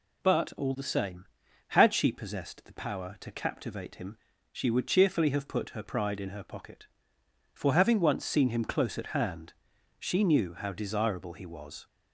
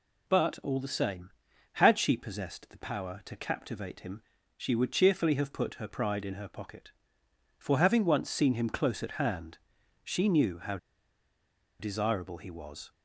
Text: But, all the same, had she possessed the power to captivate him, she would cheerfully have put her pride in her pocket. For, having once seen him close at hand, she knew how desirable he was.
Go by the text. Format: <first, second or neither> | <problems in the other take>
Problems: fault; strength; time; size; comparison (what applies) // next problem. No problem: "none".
first | pauses between "how" and "desirable"; at 10.7 s; 1.0 s long